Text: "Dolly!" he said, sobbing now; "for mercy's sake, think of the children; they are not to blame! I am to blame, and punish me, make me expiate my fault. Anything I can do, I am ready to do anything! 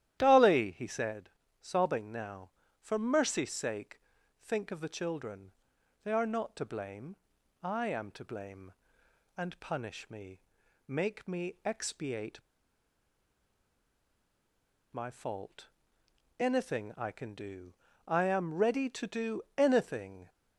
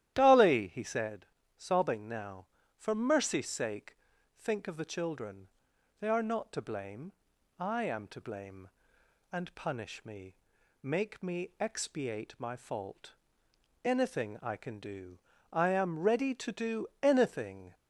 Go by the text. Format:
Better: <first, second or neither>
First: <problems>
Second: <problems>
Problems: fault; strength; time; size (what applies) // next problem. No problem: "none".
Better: second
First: starts louder than the rest; strong; until 1.2 s; 12.5 dB // pauses between "expiate" and "my"; strong; at 12.3 s; 2.5 s long // pauses between "do" and "anything"; slight; at 19.4 s; 0.16 s long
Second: starts louder than the rest; strong; until 1.1 s; 12.5 dB // pauses between "do" and "anything"; slight; at 16.8 s; 0.16 s long